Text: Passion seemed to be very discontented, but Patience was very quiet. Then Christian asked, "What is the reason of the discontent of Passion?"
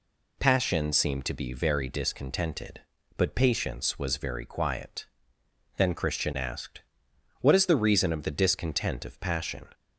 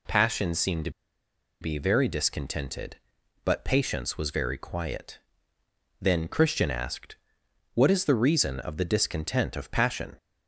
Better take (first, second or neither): first